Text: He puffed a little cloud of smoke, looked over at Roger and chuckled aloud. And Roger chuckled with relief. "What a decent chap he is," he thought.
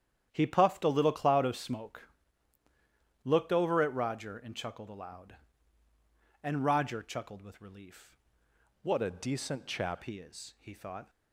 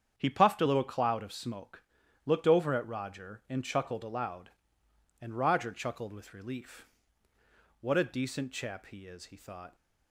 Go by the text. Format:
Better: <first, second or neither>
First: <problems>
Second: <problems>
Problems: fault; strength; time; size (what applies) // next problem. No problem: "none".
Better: second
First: starts louder than the rest; strong; until 1.3 s; 9.5 dB // changes voice from "What" to "chap"; from 8.8 to 10.0 s; 1.2 s long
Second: starts louder than the rest; strong; until 1.1 s; 8 dB